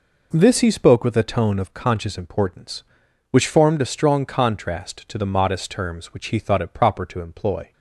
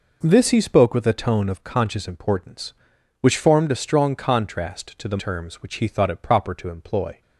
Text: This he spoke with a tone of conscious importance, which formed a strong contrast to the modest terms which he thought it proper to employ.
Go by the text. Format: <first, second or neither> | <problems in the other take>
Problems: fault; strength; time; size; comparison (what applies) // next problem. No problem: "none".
first | skips "modest"; at 5.1 s